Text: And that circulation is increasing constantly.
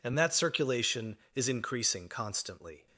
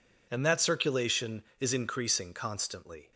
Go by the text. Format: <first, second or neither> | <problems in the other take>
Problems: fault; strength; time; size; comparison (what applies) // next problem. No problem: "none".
neither | none